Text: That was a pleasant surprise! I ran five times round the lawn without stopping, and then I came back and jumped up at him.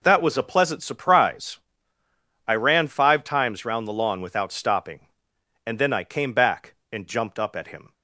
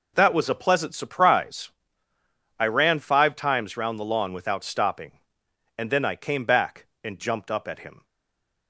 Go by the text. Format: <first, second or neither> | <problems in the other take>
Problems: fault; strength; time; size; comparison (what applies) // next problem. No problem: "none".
first | stays silent after the last word; slight; from 8.0 s on; 0.6 s long